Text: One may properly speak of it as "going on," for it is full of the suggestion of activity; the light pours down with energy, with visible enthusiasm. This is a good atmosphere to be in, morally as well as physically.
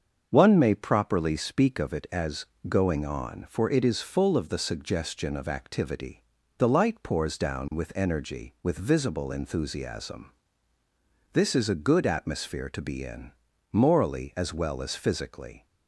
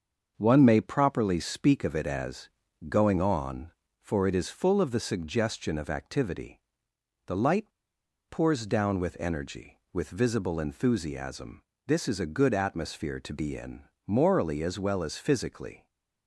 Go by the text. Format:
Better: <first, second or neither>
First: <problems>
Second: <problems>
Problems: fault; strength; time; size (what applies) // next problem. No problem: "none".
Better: first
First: starts louder than the rest; until 1.3 s; 6.5 dB // pauses between "as" and "going"; slight; at 2.4 s; 0.20 s long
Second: starts louder than the rest; until 1.3 s; 6.5 dB // pauses between "as" and "going"; at 2.4 s; 0.40 s long // pauses between "light" and "pours"; noticeable; at 7.7 s; 0.58 s long // stays silent after the last word; slight; from 15.7 s on; 0.5 s long